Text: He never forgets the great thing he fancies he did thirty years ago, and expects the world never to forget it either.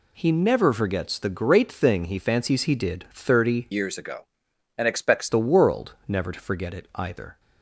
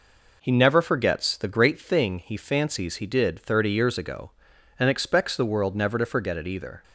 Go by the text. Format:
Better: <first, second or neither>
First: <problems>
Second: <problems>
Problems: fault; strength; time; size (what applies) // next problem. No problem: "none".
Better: second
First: changes voice from "years" to "expects"; from 3.7 to 5.2 s; 1.5 s long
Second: none